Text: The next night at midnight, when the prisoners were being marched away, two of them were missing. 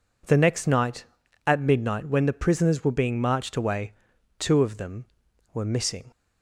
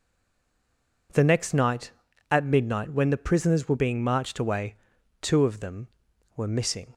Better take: first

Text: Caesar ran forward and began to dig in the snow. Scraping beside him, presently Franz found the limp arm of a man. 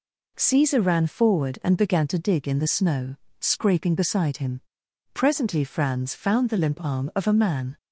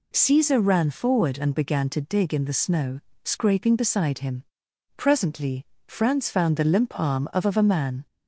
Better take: first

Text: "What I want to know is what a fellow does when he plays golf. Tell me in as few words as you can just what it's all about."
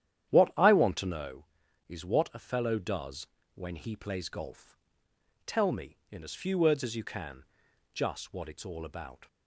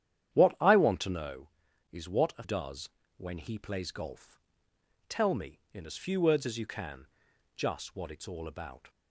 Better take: first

